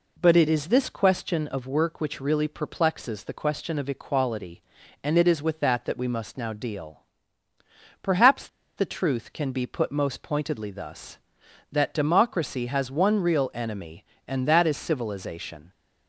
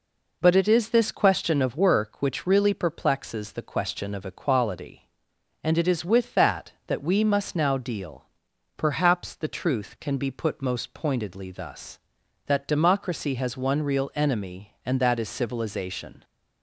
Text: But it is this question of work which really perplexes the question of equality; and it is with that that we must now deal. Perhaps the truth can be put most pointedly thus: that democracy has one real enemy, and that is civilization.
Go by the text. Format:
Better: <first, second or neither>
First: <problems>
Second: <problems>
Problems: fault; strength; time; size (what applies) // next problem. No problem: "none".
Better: second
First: pauses between "Perhaps" and "the"; slight; at 8.4 s; 0.30 s long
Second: none